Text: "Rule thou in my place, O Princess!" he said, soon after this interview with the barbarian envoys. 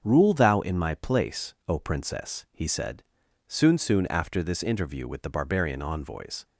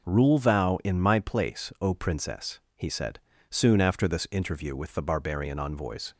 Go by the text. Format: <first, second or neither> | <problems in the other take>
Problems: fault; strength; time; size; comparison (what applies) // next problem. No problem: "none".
second | starts louder than the rest; until 1.0 s; 7 dB // says "soon" twice; at 3.7 s